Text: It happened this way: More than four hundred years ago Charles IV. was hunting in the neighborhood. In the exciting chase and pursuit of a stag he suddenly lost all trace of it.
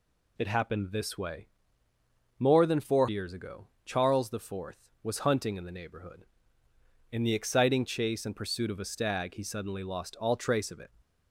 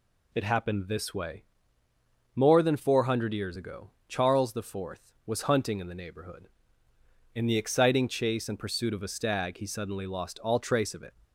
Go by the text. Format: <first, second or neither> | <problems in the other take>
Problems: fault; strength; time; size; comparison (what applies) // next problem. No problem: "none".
second | skips "hundred"; at 3.0 s // pauses between "ago" and "Charles"; slight; at 3.6 s; 0.18 s long; slight in the second